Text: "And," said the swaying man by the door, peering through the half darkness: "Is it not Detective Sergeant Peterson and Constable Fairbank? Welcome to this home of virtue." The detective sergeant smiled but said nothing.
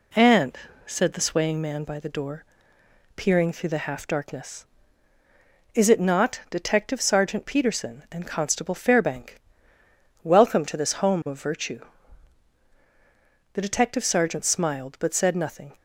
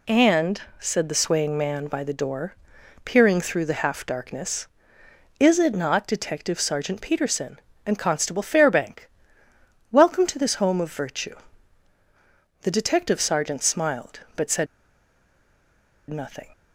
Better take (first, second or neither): first